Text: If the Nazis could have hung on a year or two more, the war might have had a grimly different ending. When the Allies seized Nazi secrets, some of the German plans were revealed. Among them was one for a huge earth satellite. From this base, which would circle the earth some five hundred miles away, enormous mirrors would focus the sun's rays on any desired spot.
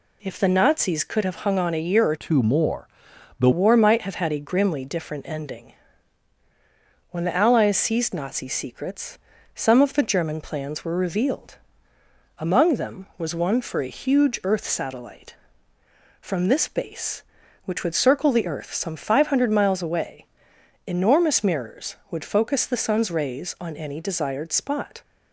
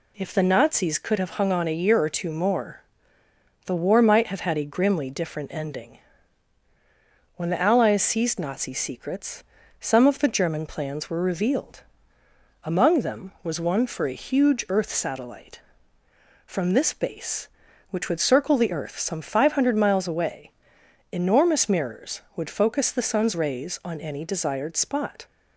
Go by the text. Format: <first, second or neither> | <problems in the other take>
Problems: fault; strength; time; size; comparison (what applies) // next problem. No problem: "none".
second | changes voice from "two" to "the"; from 2.1 to 3.4 s; 1.3 s long